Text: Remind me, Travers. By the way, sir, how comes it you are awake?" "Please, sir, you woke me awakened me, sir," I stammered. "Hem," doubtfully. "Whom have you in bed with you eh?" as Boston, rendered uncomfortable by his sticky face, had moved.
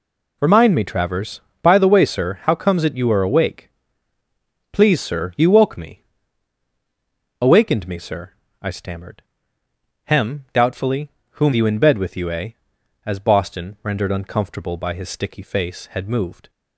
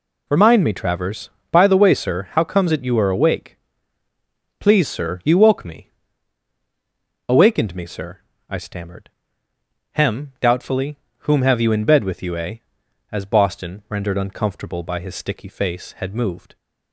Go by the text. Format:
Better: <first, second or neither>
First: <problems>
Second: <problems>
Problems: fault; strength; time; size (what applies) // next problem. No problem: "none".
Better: second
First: pauses between "me" and "awakened"; strong; at 6.0 s; 1.3 s long // skips "have"; at 11.5 s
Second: pauses between "me" and "awakened"; strong; at 5.9 s; 1.3 s long